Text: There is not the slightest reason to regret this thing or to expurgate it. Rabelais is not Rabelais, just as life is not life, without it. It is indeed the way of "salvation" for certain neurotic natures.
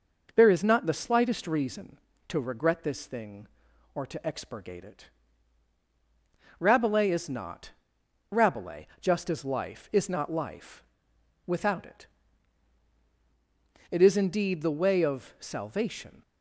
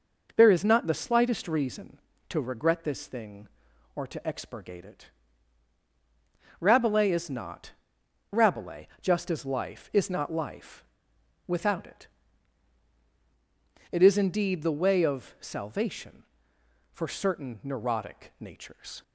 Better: second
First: pauses between "not" and "Rabelais"; noticeable; at 7.7 s; 0.60 s long // stops before "for certain neurotic natures"; at 16.2 s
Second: pauses between "not" and "Rabelais"; noticeable; at 7.7 s; 0.60 s long

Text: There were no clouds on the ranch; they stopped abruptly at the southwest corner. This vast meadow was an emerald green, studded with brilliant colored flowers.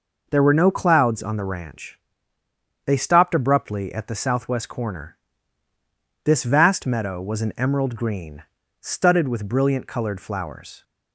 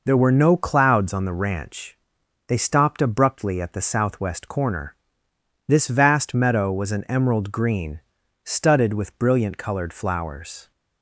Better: neither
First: none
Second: none

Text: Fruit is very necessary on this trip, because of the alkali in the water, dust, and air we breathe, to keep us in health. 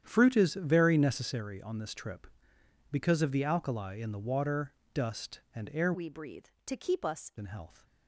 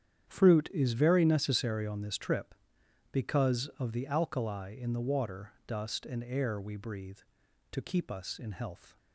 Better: second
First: starts louder than the rest; strong; until 1.0 s; 9.5 dB // changes voice from "we" to "us"; from 5.9 to 7.3 s; 1.4 s long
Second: starts louder than the rest; strong; until 1.3 s; 9 dB

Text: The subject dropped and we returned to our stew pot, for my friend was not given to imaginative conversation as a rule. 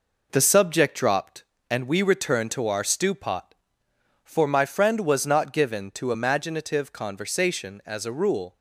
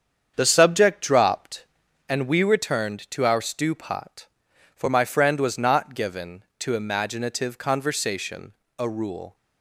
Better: first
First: none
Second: starts louder than the rest; strong; until 1.3 s; 7.5 dB // skips "as"; at 8.6 s

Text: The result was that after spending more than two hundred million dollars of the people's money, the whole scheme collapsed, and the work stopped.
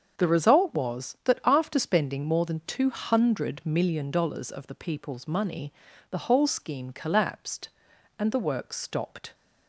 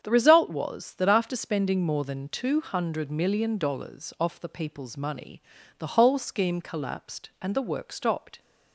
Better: first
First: starts louder than the rest; until 1.1 s; 7 dB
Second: starts louder than the rest; strong; until 1.0 s; 8 dB // says "off" for "of"; at 4.1 s

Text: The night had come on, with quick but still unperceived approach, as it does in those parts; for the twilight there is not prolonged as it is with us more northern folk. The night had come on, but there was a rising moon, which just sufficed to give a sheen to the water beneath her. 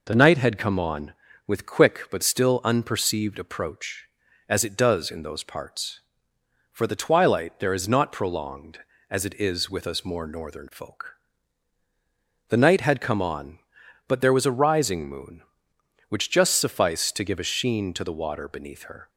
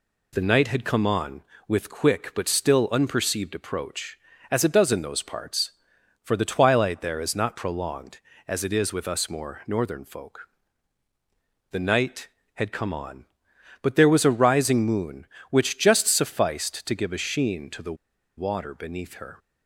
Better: first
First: none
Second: pauses between "the" and "water"; at 17.9 s; 0.43 s long

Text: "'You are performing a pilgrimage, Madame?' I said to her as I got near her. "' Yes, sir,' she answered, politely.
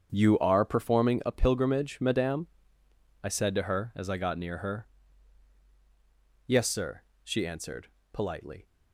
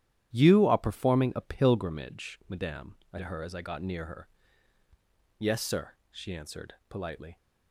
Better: first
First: starts louder than the rest; strong; until 1.1 s; 8.5 dB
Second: starts louder than the rest; strong; until 1.3 s; 11.5 dB // skips "said"; at 3.1 s

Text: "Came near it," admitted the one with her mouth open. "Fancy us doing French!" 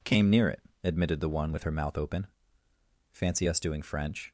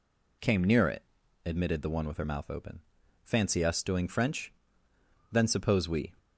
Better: first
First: none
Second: goes on to say "Then suppose we"; noticeable; from 5.3 s on; 0.80 s long

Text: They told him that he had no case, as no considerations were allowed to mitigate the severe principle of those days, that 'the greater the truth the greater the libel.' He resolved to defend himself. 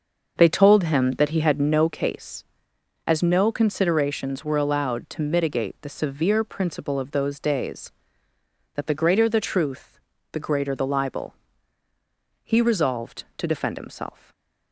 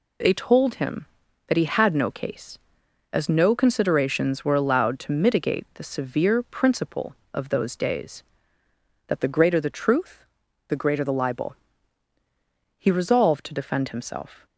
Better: second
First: starts louder than the rest; until 2.0 s; 6 dB // pauses between "truth" and "the"; slight; at 9.9 s; 0.34 s long // stays silent after the last word; slight; from 14.0 s on; 0.7 s long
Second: pauses between "truth" and "the"; at 10.2 s; 0.44 s long

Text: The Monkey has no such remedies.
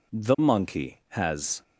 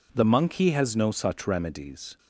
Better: second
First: stops before "no such remedies"; at 1.6 s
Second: none

